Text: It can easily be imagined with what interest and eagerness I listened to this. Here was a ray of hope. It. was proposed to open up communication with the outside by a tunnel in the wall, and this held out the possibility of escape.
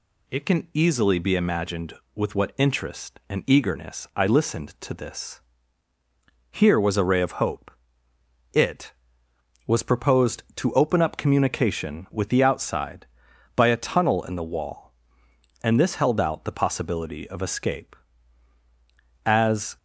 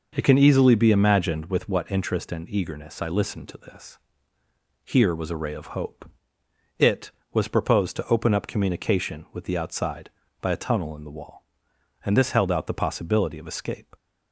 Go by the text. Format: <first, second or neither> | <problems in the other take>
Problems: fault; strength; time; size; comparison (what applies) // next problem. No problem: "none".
second | goes on to say "As"; from 19.2 s on; 0.52 s long